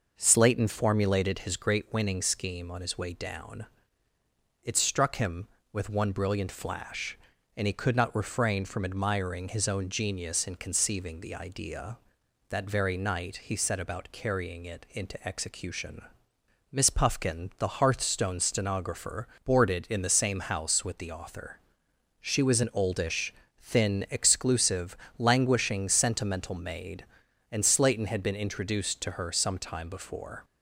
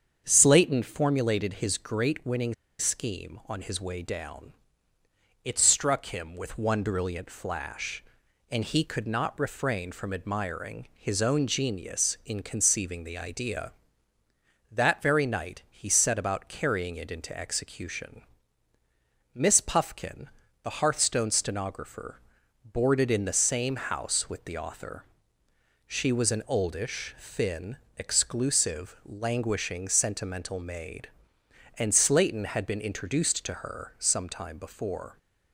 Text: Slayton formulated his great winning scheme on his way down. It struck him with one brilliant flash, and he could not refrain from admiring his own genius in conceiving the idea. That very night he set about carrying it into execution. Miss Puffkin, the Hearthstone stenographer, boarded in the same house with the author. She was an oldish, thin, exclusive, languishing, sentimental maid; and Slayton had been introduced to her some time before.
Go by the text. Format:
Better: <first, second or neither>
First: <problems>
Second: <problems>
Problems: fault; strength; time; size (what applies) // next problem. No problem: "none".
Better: first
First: none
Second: starts louder than the rest; strong; until 1.2 s; 7.5 dB // pauses between "winning" and "scheme"; slight; at 2.5 s; 0.24 s long